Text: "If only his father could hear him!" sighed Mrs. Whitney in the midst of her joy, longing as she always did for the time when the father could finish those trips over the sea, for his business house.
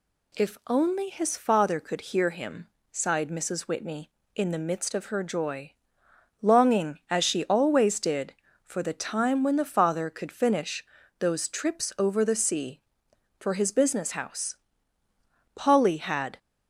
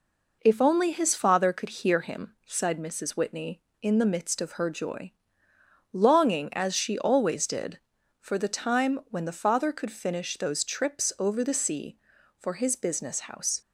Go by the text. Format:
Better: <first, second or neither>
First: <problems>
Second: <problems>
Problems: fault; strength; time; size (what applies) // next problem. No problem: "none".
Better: second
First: pauses between "finish" and "those"; slight; at 10.8 s; 0.34 s long // goes on to say "Polly had"; noticeable; from 15.5 s on; 0.82 s long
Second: none